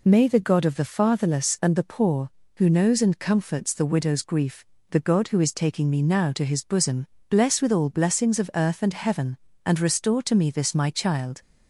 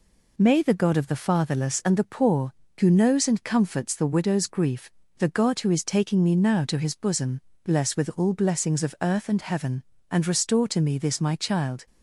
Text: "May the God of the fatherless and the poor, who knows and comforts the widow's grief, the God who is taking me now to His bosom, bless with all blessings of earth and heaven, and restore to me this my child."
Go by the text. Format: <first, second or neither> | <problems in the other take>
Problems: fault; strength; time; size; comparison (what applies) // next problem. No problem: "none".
neither | none